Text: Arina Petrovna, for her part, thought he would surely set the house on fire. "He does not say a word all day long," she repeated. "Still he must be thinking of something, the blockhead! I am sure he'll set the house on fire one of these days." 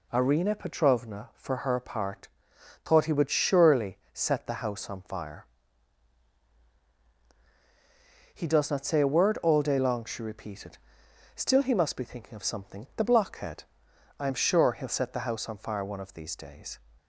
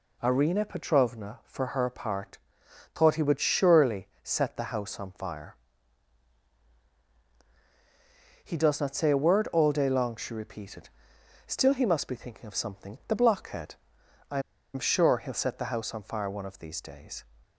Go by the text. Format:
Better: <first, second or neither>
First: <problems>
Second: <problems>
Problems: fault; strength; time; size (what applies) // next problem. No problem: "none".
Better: first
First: pauses between "surely" and "set"; slight; at 3.9 s; 0.16 s long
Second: pauses between "surely" and "set"; slight; at 4.0 s; 0.16 s long // pauses between "I" and "am"; slight; at 14.3 s; 0.34 s long